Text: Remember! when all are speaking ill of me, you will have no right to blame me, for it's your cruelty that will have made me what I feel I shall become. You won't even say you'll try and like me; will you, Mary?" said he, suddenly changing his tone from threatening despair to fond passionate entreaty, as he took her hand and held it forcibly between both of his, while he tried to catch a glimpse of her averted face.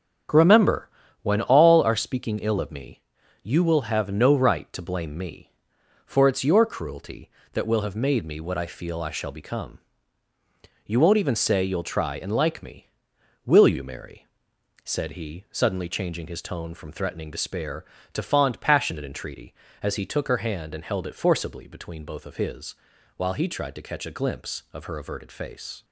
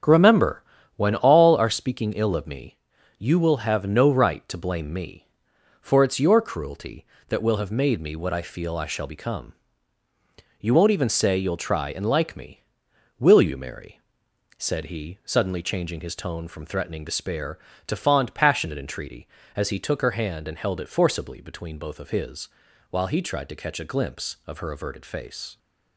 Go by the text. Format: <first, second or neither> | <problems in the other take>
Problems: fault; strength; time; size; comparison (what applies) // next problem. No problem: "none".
neither | starts louder than the rest; strong; the same in both